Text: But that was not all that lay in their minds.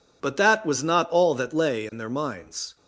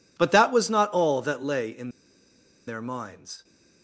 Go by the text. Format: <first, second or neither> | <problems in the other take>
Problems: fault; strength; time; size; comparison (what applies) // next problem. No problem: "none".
first | pauses between "in" and "their"; noticeable; at 1.8 s; 0.77 s long